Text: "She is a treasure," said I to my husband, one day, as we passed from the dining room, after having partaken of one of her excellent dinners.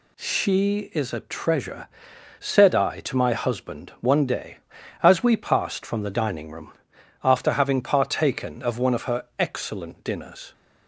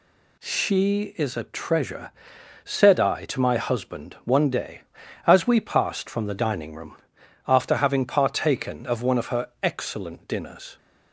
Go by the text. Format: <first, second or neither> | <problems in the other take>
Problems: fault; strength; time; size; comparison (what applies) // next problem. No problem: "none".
neither | none